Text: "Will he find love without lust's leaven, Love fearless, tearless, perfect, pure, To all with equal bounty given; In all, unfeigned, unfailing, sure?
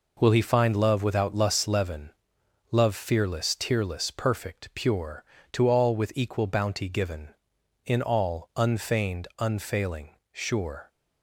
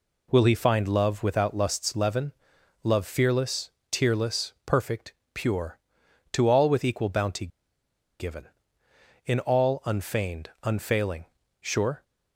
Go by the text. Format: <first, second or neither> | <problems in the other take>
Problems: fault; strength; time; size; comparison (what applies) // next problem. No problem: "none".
first | pauses between "bounty" and "given"; noticeable; at 7.4 s; 0.72 s long